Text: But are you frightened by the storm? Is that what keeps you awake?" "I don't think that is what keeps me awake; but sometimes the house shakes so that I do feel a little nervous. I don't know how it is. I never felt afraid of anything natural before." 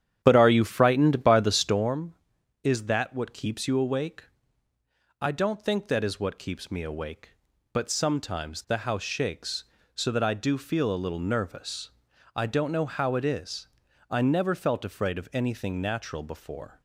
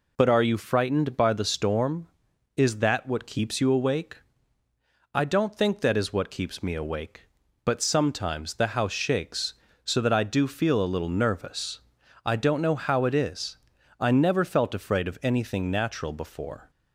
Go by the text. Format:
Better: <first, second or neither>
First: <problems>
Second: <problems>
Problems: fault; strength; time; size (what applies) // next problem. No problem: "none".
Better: second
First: starts louder than the rest; strong; until 1.9 s; 9.5 dB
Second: none